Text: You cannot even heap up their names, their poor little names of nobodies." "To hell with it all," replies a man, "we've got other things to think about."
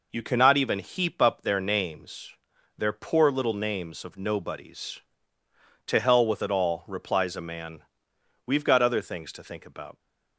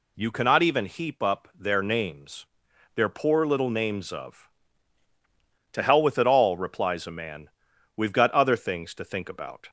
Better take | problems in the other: first | skips "nobodies"; at 5.0 s

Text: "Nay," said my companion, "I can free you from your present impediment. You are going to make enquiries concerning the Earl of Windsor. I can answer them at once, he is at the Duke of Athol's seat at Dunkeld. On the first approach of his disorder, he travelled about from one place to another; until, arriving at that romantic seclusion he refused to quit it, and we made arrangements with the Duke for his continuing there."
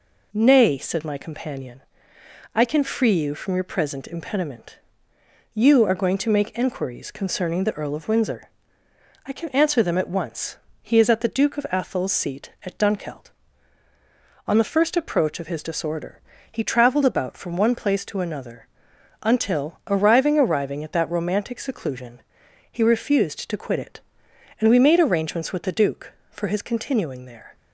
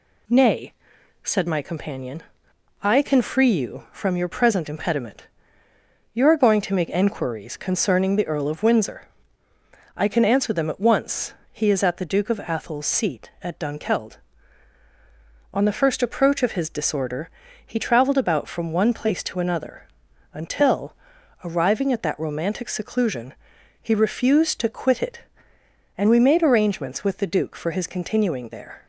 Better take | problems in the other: second | says "arriving" twice; at 20.3 s // pauses between "seclusion" and "he"; noticeable; at 22.2 s; 0.48 s long; also in the second

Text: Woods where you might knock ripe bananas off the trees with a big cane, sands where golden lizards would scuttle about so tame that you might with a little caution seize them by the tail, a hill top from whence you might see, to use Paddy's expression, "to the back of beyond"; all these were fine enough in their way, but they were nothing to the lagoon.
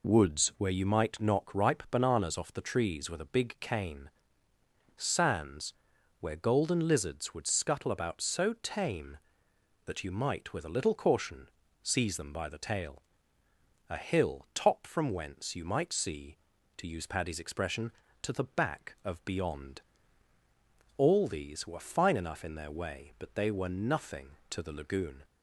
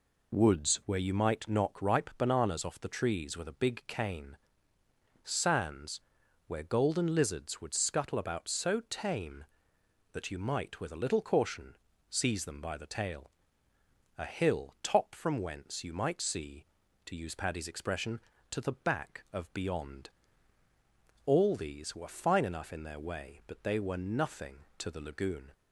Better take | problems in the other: neither | pauses between "sands" and "where"; noticeable; the same in both // pauses between "caution" and "seize"; slight; the same in both

